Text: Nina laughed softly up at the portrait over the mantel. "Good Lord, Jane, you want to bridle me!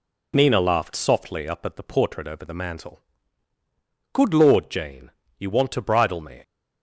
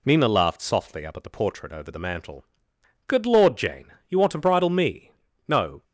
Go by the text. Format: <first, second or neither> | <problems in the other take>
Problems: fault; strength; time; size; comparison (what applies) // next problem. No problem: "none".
first | goes on to say "No"; slight; from 5.4 s on; 0.36 s long